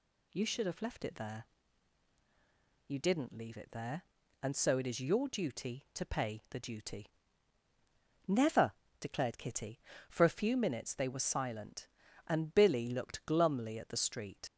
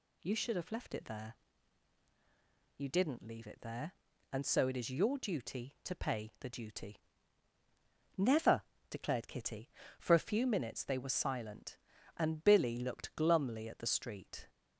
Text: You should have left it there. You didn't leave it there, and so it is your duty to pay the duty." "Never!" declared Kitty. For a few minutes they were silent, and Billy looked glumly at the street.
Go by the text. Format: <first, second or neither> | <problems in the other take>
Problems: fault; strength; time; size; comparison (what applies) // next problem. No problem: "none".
second | leaves "street" unfinished; at 14.4 s; 120 ms